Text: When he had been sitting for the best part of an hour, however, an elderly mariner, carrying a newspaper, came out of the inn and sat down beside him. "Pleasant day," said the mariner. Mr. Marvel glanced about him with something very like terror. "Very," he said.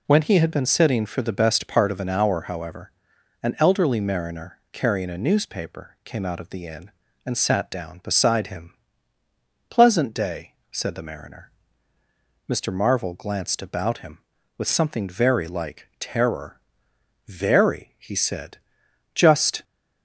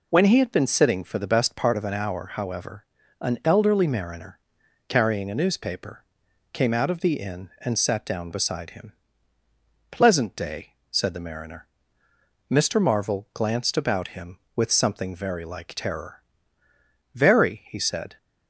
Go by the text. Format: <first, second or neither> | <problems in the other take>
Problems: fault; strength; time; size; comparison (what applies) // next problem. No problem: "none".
second | goes on to say "Just"; slight; from 19.1 s on; 0.48 s long